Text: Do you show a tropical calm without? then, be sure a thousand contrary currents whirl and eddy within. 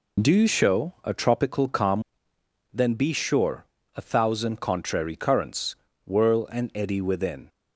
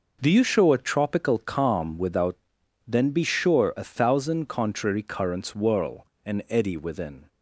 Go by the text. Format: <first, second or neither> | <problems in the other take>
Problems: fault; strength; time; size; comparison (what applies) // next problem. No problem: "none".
second | skips "without"; at 2.3 s // pauses between "sure" and "a"; slight; at 3.6 s; 0.32 s long // pauses between "currents" and "whirl"; slight; at 5.7 s; 0.30 s long